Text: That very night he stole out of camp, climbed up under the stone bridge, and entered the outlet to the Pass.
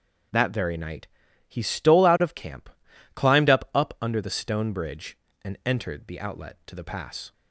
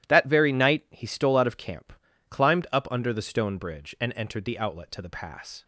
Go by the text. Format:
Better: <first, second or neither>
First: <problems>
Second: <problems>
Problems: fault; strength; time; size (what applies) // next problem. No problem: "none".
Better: second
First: starts louder than the rest; until 1.7 s; 6 dB // pauses between "night" and "he"; at 1.0 s; 0.40 s long // says "up" twice; at 3.7 s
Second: none